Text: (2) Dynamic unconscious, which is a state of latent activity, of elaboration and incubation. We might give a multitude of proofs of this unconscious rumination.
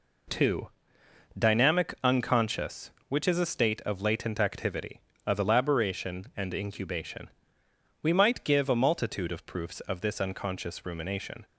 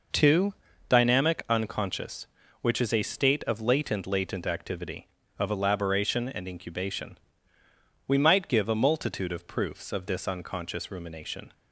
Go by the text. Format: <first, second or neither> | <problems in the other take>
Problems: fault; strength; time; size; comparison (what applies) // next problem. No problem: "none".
first | says "latent" twice; at 4.0 s